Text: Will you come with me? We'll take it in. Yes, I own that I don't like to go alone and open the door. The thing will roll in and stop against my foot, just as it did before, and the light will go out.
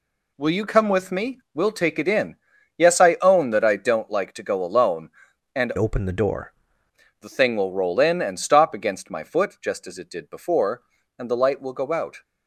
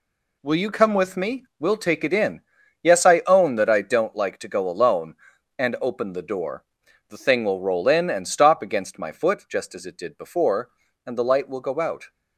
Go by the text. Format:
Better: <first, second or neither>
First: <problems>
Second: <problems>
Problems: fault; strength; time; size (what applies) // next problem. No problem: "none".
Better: second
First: changes voice from "open" to "door"; from 5.7 to 6.5 s; 0.8 s long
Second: none